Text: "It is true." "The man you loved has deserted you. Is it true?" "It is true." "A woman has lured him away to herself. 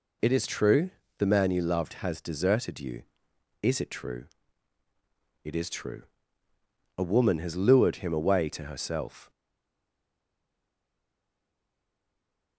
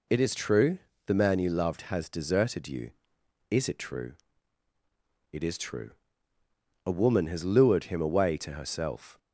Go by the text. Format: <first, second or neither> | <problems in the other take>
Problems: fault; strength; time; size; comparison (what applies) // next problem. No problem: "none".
second | stays silent after the last word; strong; from 9.2 s on; 3.3 s long